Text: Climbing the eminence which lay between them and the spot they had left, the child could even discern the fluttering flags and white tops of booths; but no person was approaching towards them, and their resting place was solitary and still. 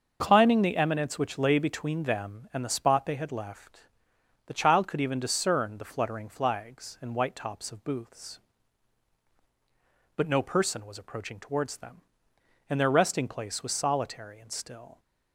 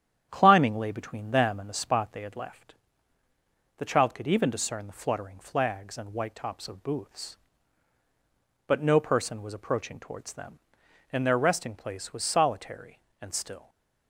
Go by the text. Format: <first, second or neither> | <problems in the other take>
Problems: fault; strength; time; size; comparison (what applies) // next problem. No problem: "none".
first | starts louder than the rest; strong; until 1.3 s; 9.5 dB; also in the first // skips "the eminence which"; at 0.7 s // stays silent after the last word; slight; from 13.5 s on; 0.5 s long